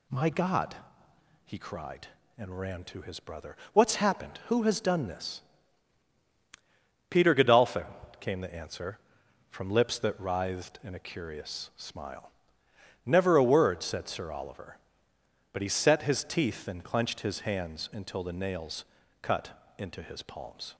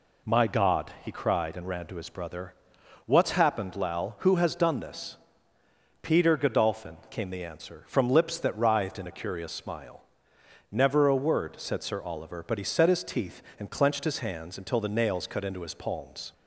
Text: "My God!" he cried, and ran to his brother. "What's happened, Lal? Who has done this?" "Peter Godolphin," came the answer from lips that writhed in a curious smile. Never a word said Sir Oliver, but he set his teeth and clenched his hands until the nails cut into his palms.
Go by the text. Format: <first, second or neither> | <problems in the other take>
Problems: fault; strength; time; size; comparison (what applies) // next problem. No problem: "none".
second | skips "Lal"; at 4.4 s // pauses between "nails" and "cut"; at 18.8 s; 0.38 s long